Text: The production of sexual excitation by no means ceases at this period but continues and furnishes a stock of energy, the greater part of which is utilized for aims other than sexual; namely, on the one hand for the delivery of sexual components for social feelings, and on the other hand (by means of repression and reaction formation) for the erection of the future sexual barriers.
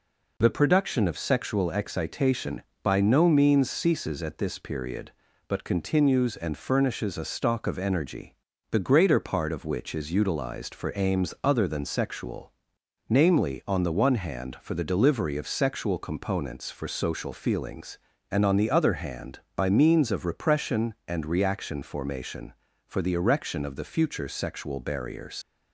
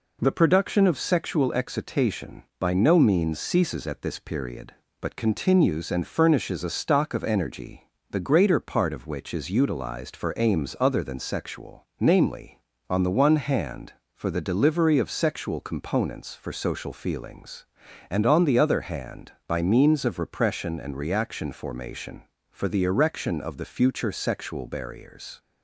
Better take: second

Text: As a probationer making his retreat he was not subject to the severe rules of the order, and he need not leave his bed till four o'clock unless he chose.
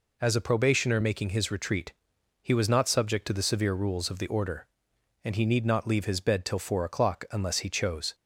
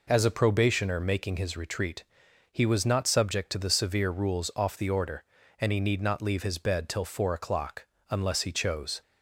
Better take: first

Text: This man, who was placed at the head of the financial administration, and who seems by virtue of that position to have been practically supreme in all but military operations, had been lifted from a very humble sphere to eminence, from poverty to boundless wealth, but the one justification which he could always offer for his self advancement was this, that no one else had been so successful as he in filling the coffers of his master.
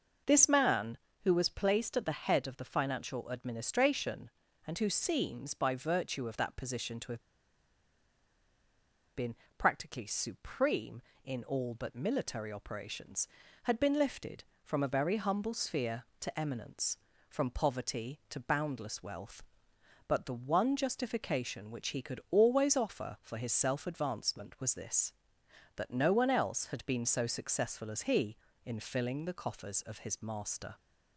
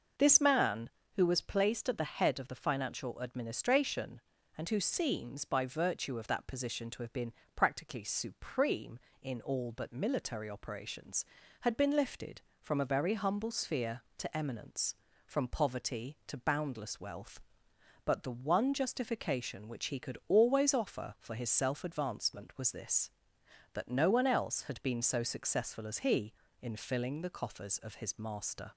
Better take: second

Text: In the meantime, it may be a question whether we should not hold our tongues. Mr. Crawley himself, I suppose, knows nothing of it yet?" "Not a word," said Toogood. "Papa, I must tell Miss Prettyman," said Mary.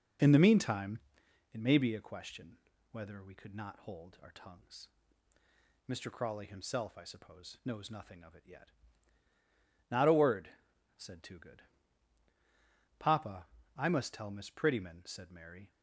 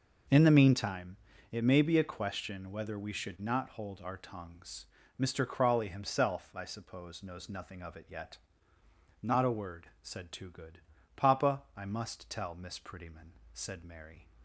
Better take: second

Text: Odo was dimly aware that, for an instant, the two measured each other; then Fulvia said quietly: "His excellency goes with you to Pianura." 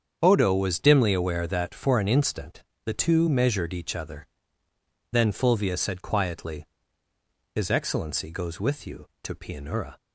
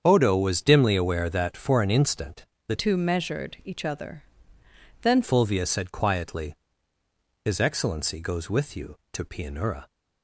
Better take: first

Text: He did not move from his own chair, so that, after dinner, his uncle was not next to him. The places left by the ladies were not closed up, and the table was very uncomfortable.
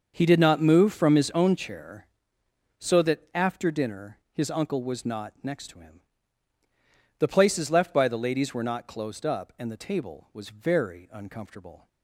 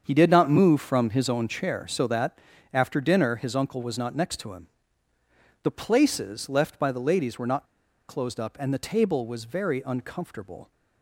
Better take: first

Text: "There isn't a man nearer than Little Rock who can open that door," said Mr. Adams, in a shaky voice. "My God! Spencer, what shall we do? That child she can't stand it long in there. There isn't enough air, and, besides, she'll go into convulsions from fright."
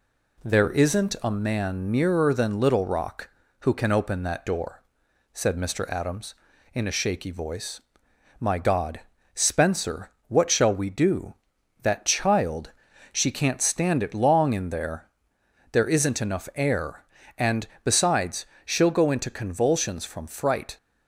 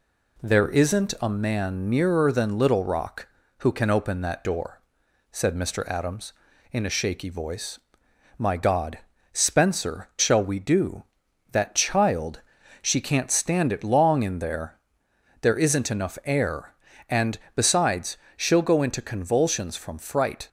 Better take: first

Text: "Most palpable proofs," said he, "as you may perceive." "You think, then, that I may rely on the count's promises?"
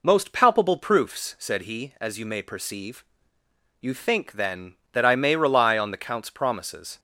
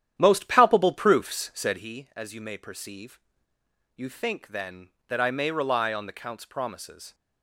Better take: first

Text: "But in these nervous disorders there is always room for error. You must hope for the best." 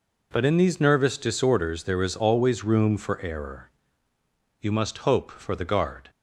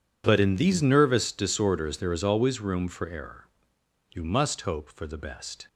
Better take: second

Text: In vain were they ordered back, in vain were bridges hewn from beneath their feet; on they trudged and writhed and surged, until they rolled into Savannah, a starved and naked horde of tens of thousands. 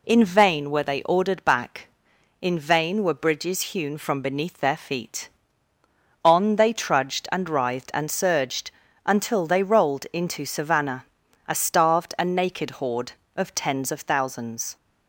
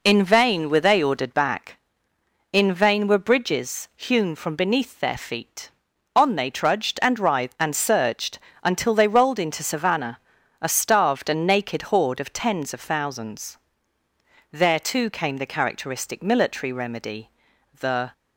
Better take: first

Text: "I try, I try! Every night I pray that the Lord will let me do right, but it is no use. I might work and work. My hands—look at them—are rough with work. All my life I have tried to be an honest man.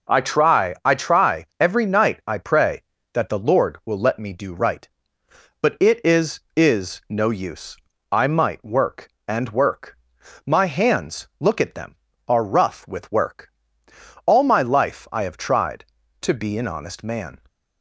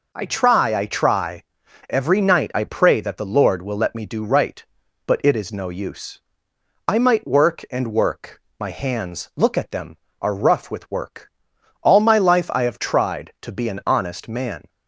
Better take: second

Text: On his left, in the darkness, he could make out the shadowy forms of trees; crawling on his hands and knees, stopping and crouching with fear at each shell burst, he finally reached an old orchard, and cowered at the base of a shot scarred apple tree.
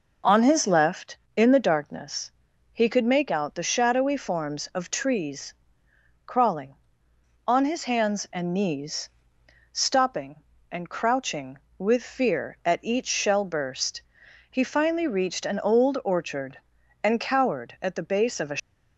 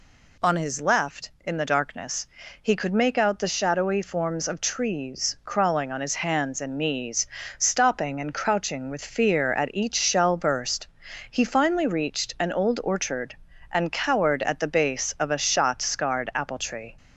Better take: second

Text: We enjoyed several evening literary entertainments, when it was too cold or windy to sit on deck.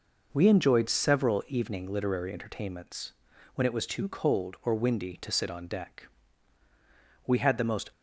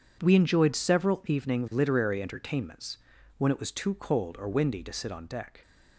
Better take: second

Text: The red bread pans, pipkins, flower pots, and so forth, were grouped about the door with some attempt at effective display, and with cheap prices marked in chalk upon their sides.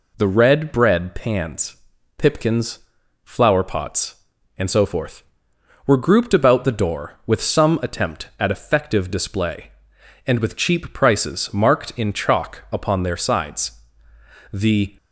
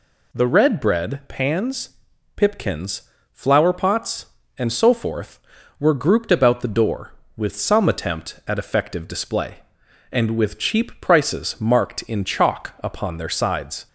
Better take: second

